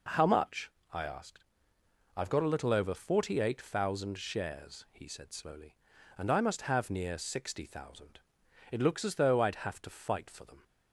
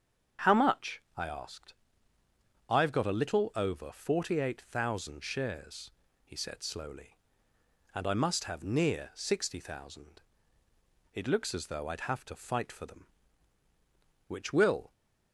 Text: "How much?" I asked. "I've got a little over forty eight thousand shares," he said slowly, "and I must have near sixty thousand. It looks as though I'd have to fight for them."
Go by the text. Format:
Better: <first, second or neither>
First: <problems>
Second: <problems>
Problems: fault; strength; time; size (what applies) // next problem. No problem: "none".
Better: first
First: none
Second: starts louder than the rest; strong; until 1.6 s; 7.5 dB // goes on to say "Which will"; noticeable; from 14.2 s on; 0.64 s long